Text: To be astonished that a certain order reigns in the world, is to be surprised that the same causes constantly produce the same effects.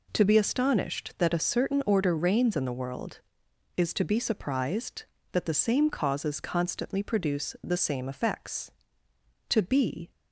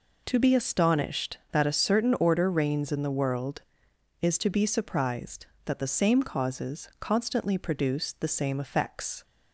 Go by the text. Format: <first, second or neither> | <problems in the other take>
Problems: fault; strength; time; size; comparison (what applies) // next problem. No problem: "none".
second | goes on to say "To be"; noticeable; from 9.4 s on; 0.62 s long